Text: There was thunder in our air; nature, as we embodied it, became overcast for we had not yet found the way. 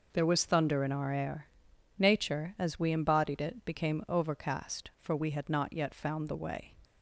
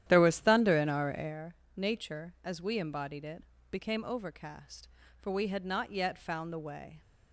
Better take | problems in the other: first | starts louder than the rest; strong; until 1.4 s; 11 dB

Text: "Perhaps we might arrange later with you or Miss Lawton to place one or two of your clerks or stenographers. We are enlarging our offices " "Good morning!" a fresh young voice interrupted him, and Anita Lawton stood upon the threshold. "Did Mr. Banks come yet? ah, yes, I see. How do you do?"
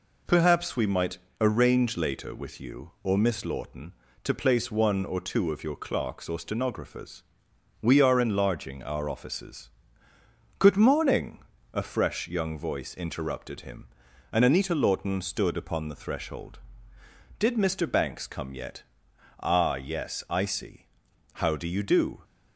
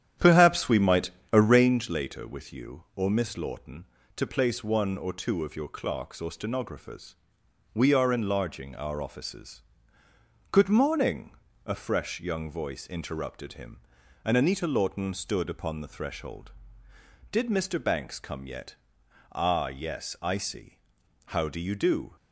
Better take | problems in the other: first | starts louder than the rest; strong; until 1.8 s; 10 dB // pauses between "might" and "arrange"; slight; at 1.1 s; 0.20 s long; slight in the first

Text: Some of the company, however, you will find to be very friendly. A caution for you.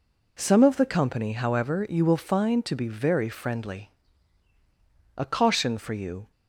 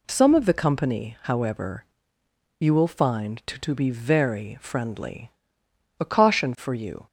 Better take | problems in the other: first | says "to" twice; at 3.5 s

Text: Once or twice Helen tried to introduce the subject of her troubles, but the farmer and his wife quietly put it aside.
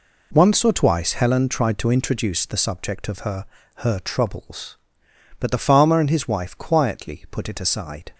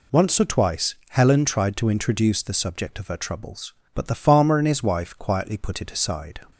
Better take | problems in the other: second | says "her" twice; at 3.7 s

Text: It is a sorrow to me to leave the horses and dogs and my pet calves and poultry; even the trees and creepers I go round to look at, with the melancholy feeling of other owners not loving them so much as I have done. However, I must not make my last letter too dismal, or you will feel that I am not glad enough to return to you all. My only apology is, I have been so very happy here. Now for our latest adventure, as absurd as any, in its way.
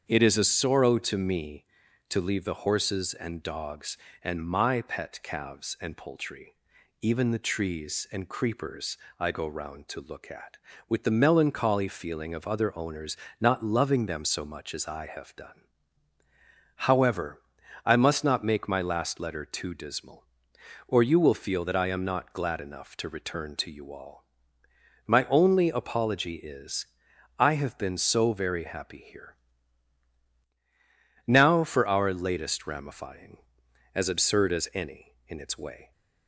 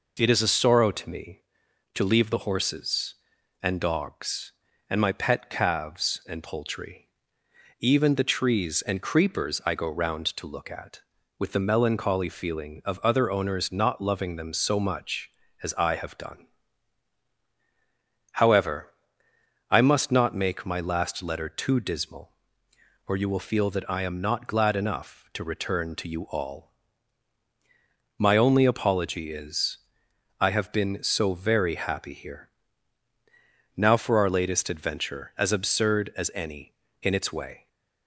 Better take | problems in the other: second | starts louder than the rest; strong; until 1.0 s; 7.5 dB // pauses between "creepers" and "I"; slight; at 8.9 s; 0.24 s long // pauses between "owners" and "not"; slight; at 13.1 s; 0.24 s long // says "ramifying" for "adventure"; at 32.6 s

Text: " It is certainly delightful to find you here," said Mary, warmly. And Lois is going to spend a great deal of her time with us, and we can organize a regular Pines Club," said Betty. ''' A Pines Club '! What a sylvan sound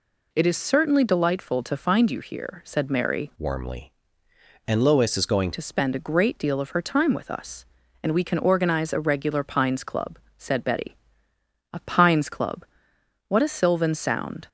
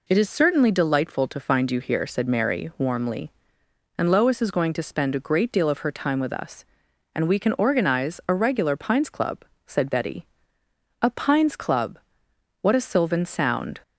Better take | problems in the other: second | changes voice from "warmly" to "going"; from 3.3 to 5.5 s; 2.2 s long

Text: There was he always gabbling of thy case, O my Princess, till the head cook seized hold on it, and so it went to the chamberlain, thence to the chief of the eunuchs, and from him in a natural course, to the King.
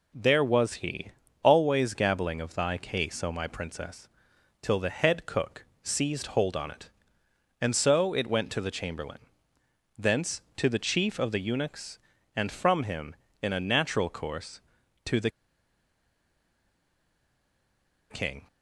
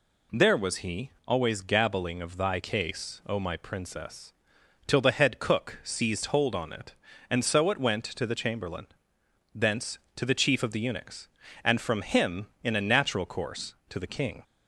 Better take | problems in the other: second | pauses between "he" and "always"; slight; at 1.1 s; 0.30 s long; slight in the second // pauses between "cook" and "seized"; slight; at 5.6 s; 0.18 s long // pauses between "the" and "King"; strong; at 15.2 s; 2.8 s long

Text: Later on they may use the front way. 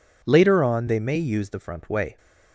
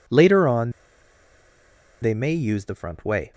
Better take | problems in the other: first | pauses between "on" and "they"; strong; at 0.7 s; 1.3 s long

